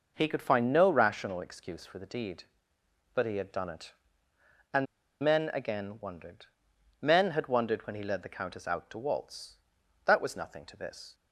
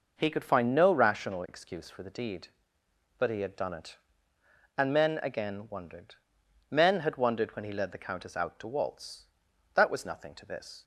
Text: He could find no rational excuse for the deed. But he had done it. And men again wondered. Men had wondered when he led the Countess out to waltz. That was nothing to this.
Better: second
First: pauses between "And" and "men"; at 4.8 s; 0.36 s long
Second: none

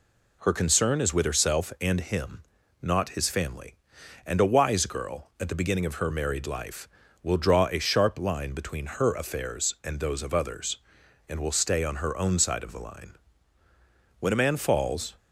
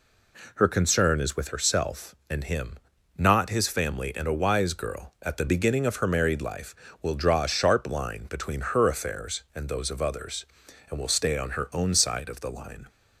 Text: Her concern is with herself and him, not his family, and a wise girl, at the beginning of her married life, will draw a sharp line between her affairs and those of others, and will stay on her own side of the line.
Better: second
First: goes on to say "When a man falls"; noticeable; from 14.2 s on; 0.94 s long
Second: none

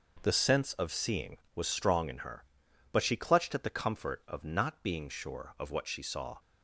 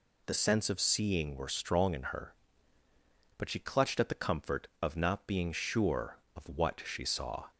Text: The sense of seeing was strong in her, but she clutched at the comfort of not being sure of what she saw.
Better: first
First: none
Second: says "were" for "was"; at 1.3 s

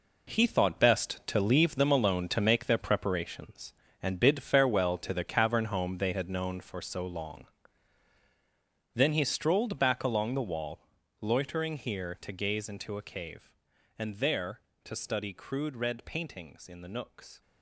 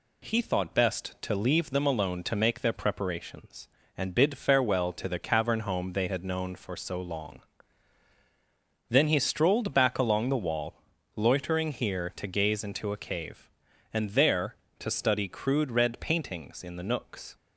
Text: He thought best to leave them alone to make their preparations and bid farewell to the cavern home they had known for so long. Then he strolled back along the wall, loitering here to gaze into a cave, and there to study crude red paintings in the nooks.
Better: second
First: gets quieter; strong; throughout; 10.5 dB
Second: none

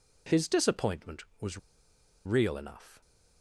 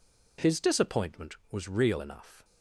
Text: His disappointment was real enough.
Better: second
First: pauses between "was" and "real"; noticeable; at 1.5 s; 0.68 s long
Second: none

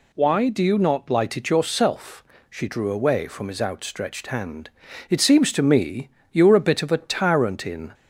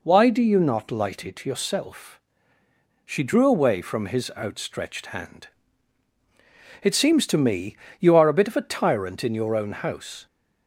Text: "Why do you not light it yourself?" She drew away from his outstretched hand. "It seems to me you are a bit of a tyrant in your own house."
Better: second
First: pauses between "me" and "you"; slight; at 6.0 s; 0.24 s long // stops before "your own house"; at 7.9 s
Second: pauses between "me" and "you"; slight; at 7.7 s; 0.22 s long

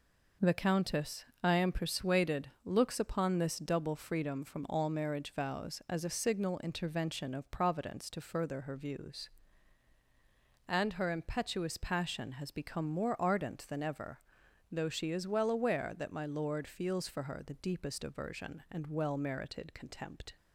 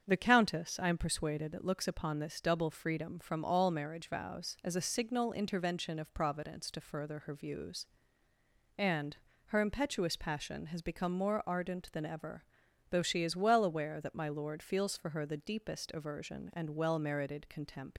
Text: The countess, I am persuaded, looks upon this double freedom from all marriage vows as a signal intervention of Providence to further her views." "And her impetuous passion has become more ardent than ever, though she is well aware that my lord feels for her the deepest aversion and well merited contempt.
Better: first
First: none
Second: starts louder than the rest; strong; until 1.0 s; 7.5 dB // pauses between "And" and "her"; slight; at 9.1 s; 0.30 s long // leaves "contempt" unfinished; at 17.9 s; 115 ms

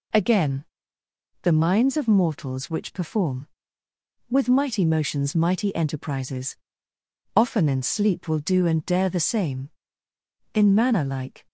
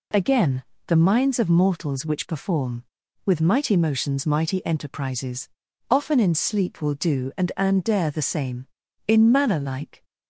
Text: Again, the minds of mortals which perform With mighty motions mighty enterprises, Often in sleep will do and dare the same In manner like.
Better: first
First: none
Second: says "and" twice; at 7.5 s

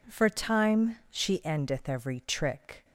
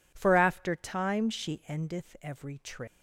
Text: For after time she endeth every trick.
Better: second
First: skips "after"; at 0.2 s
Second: none

